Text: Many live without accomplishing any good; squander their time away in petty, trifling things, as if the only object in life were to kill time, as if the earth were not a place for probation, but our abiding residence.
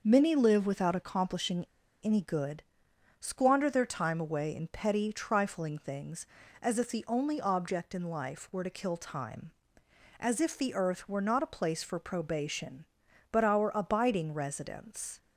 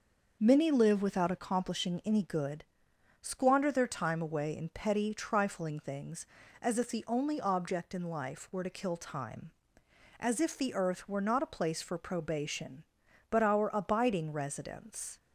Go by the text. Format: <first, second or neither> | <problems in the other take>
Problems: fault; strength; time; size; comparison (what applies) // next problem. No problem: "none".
second | pauses between "accomplishing" and "any"; at 1.6 s; 0.36 s long